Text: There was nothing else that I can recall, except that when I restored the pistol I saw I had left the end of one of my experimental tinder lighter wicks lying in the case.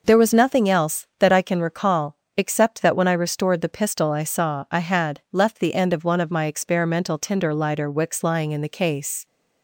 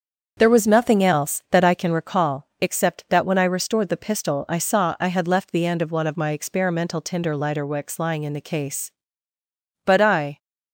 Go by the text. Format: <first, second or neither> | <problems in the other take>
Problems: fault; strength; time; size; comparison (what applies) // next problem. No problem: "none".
first | starts louder than the rest; until 1.3 s; 7 dB // goes on to say "But I"; from 9.8 s on; 0.54 s long